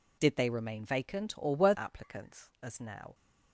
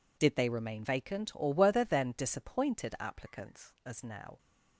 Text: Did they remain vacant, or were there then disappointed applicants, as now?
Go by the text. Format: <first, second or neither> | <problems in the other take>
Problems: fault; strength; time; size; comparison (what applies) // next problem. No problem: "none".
second | skips "there then disappointed"; at 1.7 s